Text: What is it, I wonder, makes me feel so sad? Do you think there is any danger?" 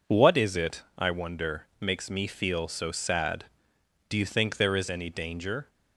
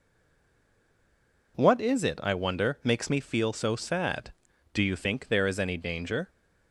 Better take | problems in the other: first | stays silent before the first word; noticeable; until 1.5 s; 1.5 s long

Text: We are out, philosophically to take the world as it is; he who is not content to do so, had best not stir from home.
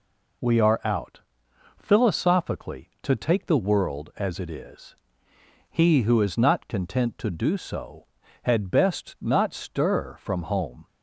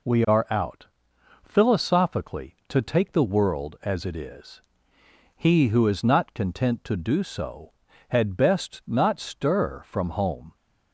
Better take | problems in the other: neither | none

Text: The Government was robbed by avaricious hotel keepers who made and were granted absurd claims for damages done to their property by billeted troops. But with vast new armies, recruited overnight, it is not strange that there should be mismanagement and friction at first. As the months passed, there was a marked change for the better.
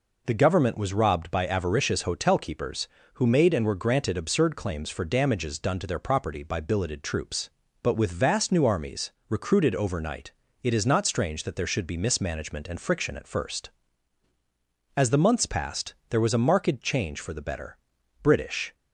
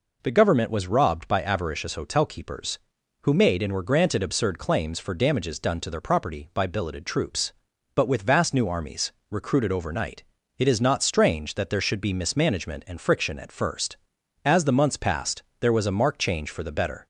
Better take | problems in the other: second | goes on to say "British"; from 18.2 s on; 0.52 s long

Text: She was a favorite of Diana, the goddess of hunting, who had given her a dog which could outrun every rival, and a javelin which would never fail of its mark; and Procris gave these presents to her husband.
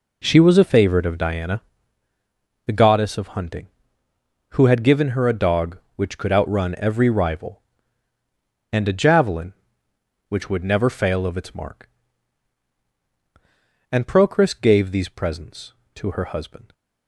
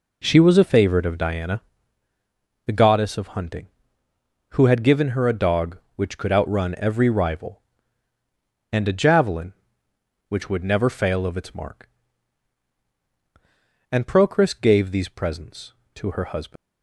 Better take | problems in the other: first | leaves "husband" unfinished; at 16.5 s; 170 ms

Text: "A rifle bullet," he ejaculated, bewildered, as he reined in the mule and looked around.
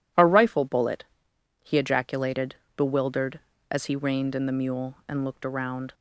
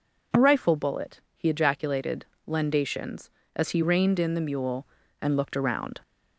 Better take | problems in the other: first | says "lendations" for "bewildered"; at 2.4 s

